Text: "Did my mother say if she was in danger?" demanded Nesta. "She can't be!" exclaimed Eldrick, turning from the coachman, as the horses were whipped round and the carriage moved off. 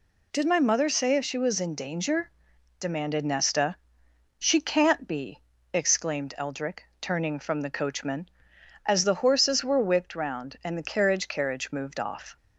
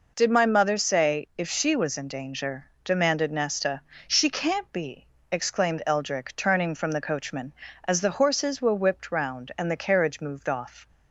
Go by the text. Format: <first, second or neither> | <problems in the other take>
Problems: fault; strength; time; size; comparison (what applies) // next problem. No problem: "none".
second | says "carriage" twice; at 11.2 s